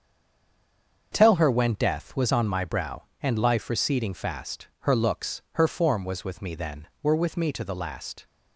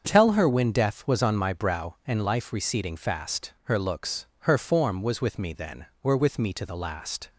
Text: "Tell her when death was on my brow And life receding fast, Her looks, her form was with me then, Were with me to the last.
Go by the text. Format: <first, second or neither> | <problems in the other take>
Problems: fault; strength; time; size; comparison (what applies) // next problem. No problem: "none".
second | stays silent before the first word; until 1.1 s; 1.1 s long // starts louder than the rest; until 2.1 s; 7 dB; also in the second